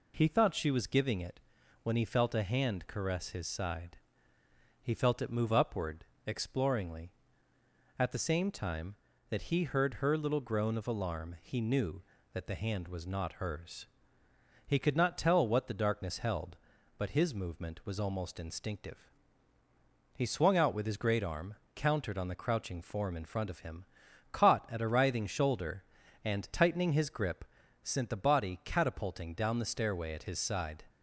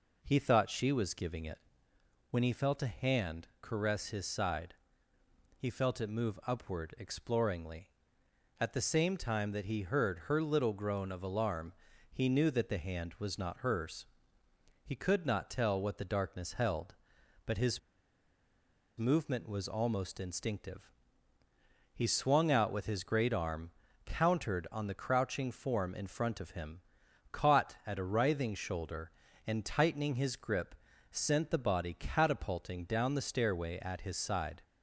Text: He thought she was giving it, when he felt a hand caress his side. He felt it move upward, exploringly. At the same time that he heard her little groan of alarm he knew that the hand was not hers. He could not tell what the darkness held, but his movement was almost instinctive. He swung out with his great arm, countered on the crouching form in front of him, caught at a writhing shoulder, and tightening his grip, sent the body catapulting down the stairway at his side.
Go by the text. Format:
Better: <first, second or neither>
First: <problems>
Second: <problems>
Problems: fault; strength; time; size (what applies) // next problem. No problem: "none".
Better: first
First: none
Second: pauses between "alarm" and "he"; at 11.7 s; 0.40 s long // pauses between "his" and "movement"; at 17.7 s; 1.1 s long